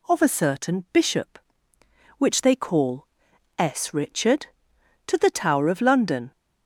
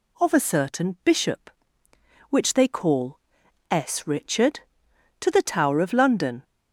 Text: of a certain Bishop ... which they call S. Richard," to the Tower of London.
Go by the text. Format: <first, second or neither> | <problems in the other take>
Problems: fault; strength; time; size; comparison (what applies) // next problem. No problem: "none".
neither | pauses between "call" and "S"; noticeable; the same in both